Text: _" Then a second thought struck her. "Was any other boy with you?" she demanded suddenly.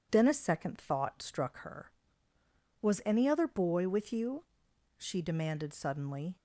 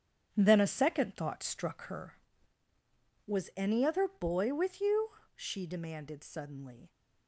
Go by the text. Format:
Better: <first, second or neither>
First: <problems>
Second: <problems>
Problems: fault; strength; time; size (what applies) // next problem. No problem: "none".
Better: first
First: none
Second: gets quieter; strong; throughout; 8.5 dB